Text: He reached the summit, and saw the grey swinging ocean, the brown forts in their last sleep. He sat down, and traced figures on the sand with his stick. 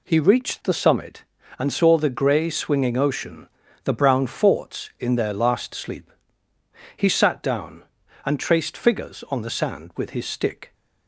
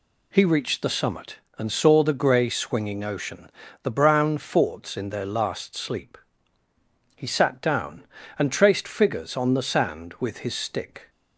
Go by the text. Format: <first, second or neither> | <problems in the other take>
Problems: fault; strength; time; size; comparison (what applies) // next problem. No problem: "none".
neither | none